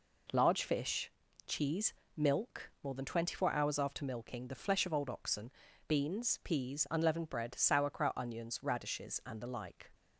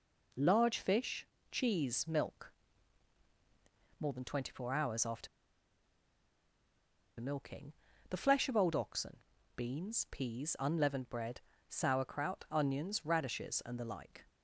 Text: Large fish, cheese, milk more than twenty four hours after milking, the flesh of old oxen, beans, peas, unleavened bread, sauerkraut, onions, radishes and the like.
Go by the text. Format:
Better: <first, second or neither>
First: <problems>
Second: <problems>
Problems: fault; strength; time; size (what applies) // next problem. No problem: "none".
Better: first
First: none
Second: pauses between "milk" and "more"; strong; at 2.4 s; 1.5 s long // pauses between "after" and "milking"; strong; at 5.2 s; 1.9 s long